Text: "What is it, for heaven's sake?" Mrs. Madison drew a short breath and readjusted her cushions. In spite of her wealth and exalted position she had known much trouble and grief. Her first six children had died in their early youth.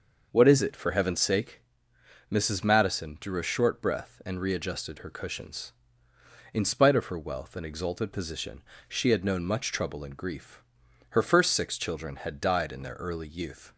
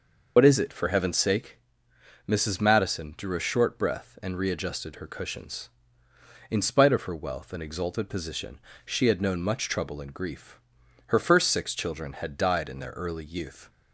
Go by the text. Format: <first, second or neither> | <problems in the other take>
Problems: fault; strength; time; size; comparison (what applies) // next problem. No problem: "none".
first | loses the start of "What"; at 0.3 s; 75 ms // pauses between "position" and "she"; slight; at 8.5 s; 0.26 s long; slight in the first